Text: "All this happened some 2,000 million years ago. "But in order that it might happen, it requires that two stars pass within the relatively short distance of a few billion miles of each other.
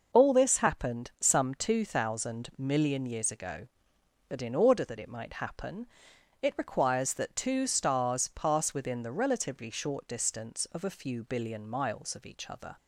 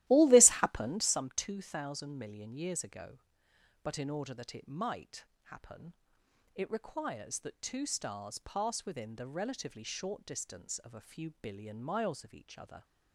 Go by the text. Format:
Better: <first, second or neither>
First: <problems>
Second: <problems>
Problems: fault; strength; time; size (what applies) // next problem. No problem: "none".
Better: first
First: none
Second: starts louder than the rest; strong; until 1.2 s; 15 dB // pauses between "might" and "happen"; slight; at 5.2 s; 0.22 s long